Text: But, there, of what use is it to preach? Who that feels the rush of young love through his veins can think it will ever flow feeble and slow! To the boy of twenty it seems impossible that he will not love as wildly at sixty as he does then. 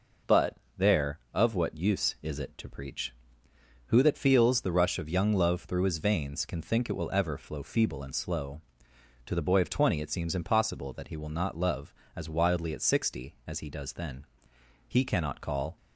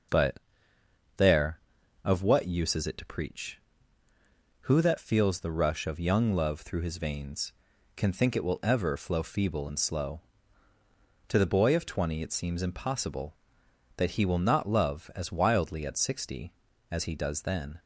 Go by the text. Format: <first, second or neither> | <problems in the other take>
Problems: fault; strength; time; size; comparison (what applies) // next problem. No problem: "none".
second | goes on to say "He cannot call"; noticeable; from 14.8 s on; 0.90 s long